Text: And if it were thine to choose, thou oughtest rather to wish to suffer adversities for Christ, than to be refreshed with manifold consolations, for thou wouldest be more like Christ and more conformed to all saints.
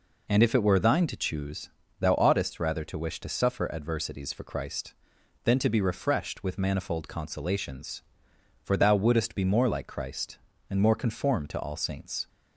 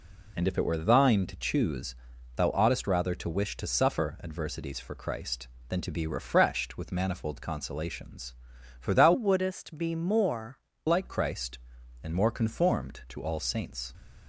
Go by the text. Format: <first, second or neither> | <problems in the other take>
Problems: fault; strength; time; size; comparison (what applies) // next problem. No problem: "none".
first | changes voice from "wouldest" to "more"; from 9.1 to 10.5 s; 1.4 s long